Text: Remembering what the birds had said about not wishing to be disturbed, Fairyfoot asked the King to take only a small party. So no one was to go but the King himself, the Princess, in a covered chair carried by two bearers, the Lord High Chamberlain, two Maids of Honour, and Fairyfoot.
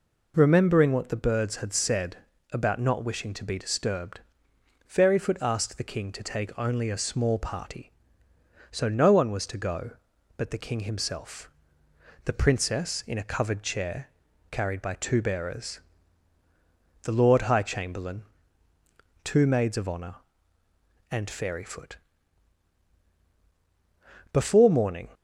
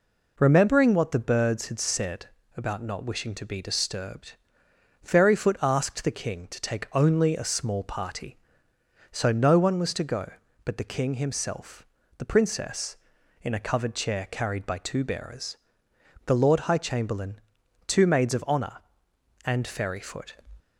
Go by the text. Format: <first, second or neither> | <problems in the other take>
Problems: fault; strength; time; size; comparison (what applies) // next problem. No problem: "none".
second | pauses between "said" and "about"; slight; at 2.1 s; 0.34 s long; slight in the second // pauses between "chair" and "carried"; at 14.0 s; 0.42 s long // goes on to say "Before morning"; noticeable; from 24.3 s on; 0.82 s long